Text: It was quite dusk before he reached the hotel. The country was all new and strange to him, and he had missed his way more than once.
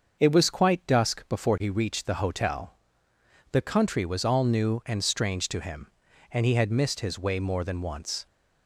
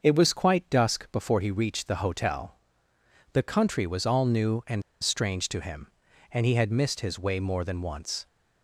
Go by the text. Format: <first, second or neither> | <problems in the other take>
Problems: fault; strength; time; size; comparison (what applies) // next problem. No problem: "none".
first | starts louder than the rest; until 1.0 s; 6.5 dB; also in the first // pauses between "and" and "strange"; slight; at 4.8 s; 0.21 s long